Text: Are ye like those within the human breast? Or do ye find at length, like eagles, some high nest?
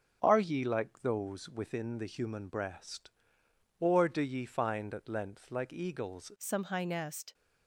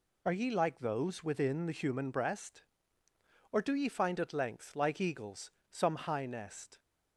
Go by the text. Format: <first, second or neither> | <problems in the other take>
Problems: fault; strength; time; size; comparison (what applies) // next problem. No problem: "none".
second | changes voice at "some"; from 6.3 s on; 1.0 s long